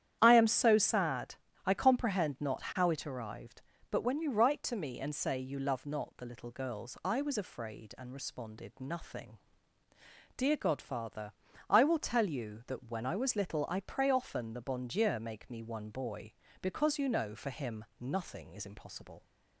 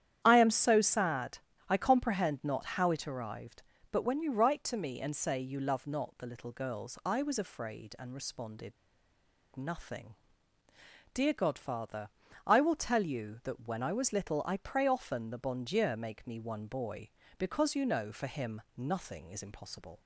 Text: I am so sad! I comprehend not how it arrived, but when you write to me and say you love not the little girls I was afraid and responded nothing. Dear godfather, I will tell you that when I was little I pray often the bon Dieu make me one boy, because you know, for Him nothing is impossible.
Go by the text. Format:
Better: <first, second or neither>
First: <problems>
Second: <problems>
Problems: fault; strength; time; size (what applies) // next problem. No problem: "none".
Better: first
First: starts louder than the rest; strong; until 1.2 s; 10 dB // pauses between "Him" and "nothing"; slight; at 17.8 s; 0.16 s long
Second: starts louder than the rest; strong; until 1.2 s; 10 dB // pauses between "responded" and "nothing"; noticeable; at 8.7 s; 0.84 s long // pauses between "Him" and "nothing"; slight; at 18.6 s; 0.16 s long